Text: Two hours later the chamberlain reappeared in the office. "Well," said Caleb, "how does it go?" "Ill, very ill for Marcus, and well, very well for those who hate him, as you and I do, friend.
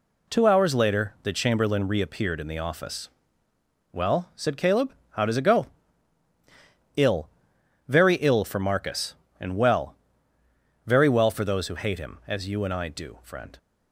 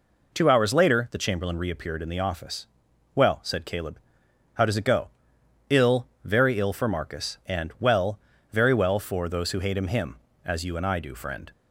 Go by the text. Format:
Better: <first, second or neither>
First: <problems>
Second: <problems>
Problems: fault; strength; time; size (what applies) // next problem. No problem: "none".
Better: first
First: none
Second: says "him" twice; at 9.8 s